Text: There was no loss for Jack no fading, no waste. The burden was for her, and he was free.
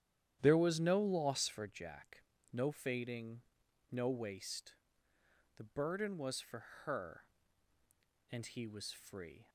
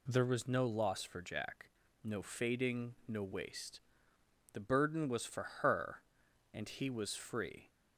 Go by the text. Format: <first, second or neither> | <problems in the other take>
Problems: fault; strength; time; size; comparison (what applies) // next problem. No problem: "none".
second | starts louder than the rest; strong; until 1.7 s; 10.5 dB // pauses between "Jack" and "no"; slight; at 2.2 s; 0.32 s long; also in the second // pauses between "for" and "her"; slight; at 6.6 s; 0.22 s long; slight in the second